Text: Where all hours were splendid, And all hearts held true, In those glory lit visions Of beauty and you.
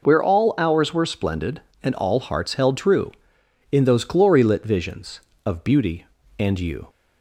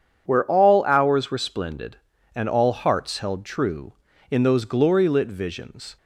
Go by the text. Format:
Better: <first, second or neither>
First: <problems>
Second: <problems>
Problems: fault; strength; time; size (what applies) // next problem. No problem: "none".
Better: first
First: none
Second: stops before "Of beauty and you"; at 5.9 s